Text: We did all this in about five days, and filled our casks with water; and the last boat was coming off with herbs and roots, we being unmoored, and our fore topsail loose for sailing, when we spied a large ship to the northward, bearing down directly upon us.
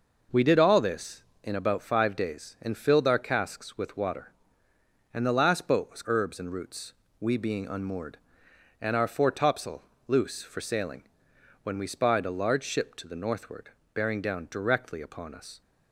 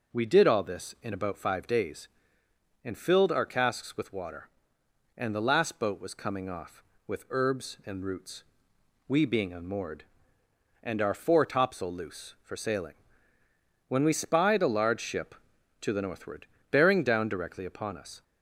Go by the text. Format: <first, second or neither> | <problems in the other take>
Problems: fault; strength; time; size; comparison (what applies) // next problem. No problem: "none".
second | skips "coming off with"; at 6.0 s // pauses between "topsail" and "loose"; slight; at 9.8 s; 0.24 s long